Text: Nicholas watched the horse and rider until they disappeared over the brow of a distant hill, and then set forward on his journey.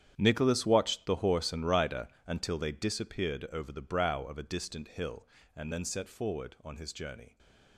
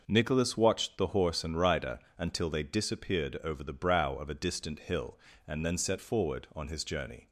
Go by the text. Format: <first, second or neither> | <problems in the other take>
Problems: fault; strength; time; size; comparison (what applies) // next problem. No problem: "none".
second | gets quieter; strong; throughout; 15 dB // pauses between "rider" and "until"; slight; at 2.0 s; 0.22 s long; slight in the second